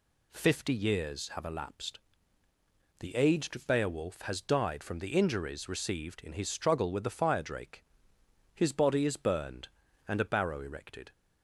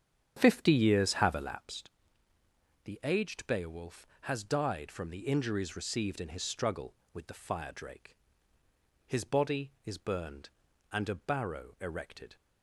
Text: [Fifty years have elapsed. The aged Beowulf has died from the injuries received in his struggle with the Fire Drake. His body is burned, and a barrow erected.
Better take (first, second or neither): first